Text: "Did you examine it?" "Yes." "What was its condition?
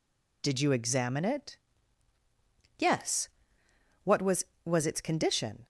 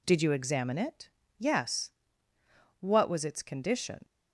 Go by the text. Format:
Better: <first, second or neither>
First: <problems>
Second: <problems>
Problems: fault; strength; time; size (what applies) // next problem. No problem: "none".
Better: second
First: says "was" twice; at 4.6 s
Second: none